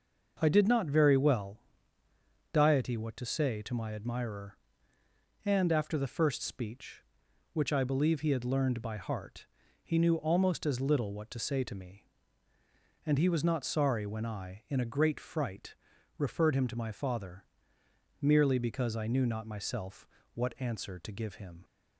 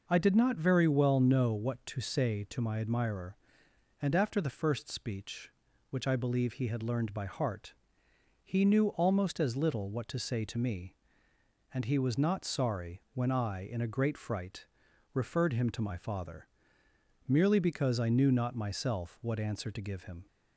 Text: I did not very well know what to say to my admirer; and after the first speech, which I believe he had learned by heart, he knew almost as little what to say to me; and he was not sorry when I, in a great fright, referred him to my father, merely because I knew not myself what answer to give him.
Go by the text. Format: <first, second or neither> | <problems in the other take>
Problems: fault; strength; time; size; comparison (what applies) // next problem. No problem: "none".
second | starts louder than the rest; noticeable; until 1.4 s; 6 dB // says "diety" for "know"; at 2.5 s // pauses between "myself" and "what"; slight; at 20.0 s; 0.30 s long